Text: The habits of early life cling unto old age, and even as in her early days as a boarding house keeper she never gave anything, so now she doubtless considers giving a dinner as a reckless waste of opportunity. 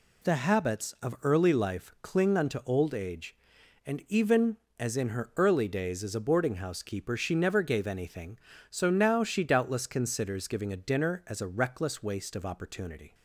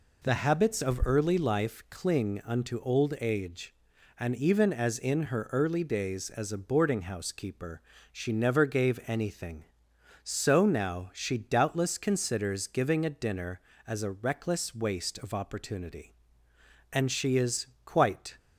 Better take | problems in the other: first | pauses between "keeper" and "she"; slight; at 7.8 s; 0.32 s long // goes on to say "And she is quite"; from 16.9 s on; 1.4 s long

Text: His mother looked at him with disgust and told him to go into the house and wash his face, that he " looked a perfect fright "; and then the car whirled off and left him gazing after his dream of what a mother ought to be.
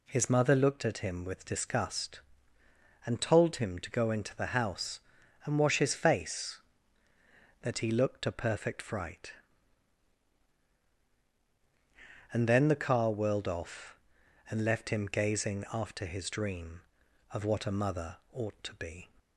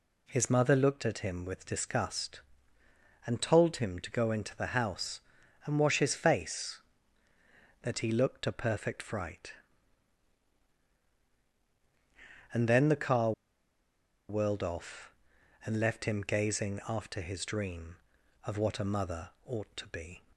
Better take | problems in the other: first | pauses between "car" and "whirled"; noticeable; at 13.3 s; 0.97 s long // pauses between "mother" and "ought"; slight; at 19.3 s; 0.16 s long; slight in the first

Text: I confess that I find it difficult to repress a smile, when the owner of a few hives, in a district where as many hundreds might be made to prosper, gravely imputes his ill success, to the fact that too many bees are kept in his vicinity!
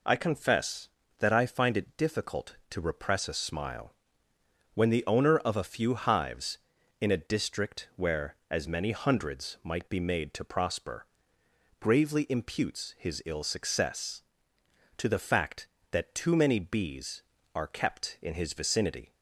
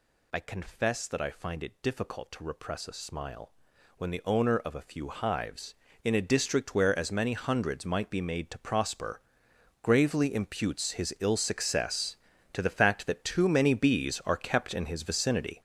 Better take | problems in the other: first | gets louder; strong; throughout; 9.5 dB

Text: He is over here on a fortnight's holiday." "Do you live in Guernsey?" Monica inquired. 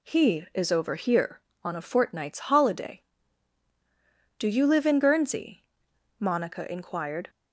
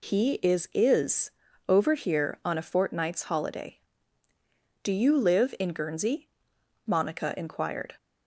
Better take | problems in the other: first | says "is" twice; at 0.7 s

